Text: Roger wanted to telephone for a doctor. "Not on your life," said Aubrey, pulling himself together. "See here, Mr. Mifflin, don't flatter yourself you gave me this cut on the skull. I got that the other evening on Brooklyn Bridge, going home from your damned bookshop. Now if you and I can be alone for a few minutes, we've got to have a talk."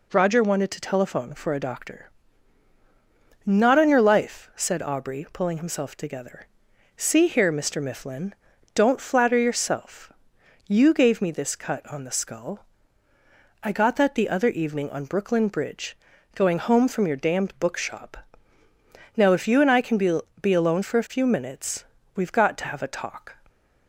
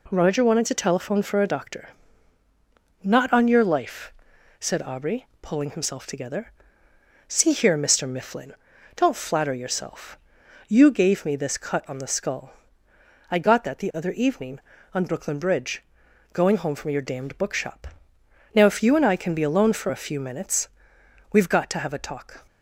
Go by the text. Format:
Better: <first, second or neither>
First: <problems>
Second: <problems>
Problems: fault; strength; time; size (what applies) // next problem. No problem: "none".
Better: second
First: pauses between "yourself" and "you"; noticeable; at 10.1 s; 0.58 s long // says "be" twice; at 20.4 s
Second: pauses between "yourself" and "you"; noticeable; at 10.1 s; 0.52 s long